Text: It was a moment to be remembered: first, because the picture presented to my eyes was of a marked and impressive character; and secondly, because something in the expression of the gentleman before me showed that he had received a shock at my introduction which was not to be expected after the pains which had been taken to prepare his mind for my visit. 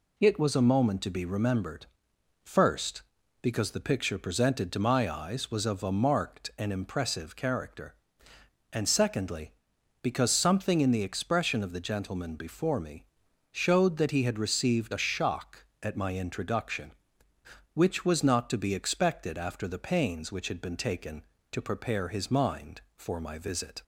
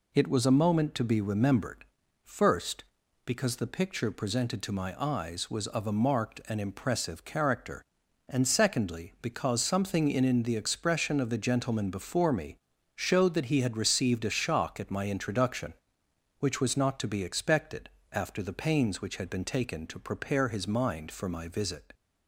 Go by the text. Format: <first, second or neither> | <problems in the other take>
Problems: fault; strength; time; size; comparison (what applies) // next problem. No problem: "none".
first | says "in" twice; at 10.2 s // pauses between "me" and "showed"; at 12.5 s; 0.38 s long; noticeable in the first // pauses between "expected" and "after"; slight; at 17.8 s; 0.23 s long